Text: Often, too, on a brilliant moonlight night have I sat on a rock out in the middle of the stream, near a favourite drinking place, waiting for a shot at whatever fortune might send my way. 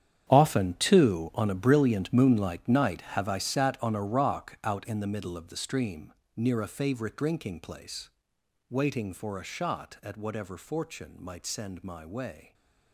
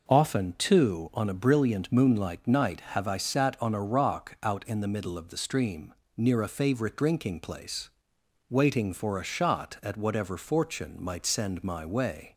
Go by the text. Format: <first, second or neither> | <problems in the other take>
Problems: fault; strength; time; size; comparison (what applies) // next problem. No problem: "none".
second | gets quieter; strong; throughout; 15 dB